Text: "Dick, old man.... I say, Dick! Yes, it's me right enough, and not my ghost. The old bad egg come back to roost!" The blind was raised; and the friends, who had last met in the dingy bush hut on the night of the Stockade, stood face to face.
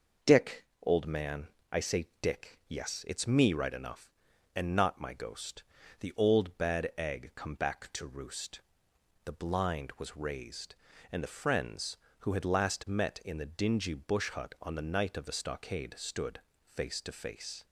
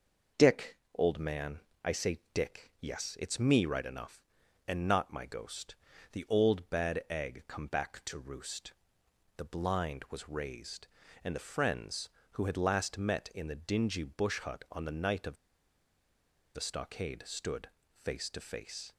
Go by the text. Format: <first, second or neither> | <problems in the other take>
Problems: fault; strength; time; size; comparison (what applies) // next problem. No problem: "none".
first | pauses between "of" and "the"; at 15.3 s; 1.1 s long // pauses between "stood" and "face"; slight; at 17.6 s; 0.30 s long; slight in the first